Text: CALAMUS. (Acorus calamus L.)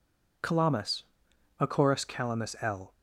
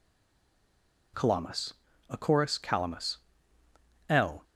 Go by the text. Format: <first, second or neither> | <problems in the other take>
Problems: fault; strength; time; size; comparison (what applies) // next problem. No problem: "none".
first | stays silent before the first word; until 1.1 s; 1.1 s long // pauses between "calamus" and "L"; noticeable; at 3.1 s; 0.92 s long